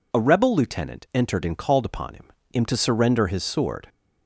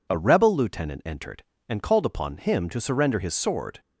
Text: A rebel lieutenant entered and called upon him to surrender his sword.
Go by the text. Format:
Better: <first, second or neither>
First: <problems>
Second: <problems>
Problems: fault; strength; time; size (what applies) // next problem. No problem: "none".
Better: second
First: says "him" twice; at 2.5 s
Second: none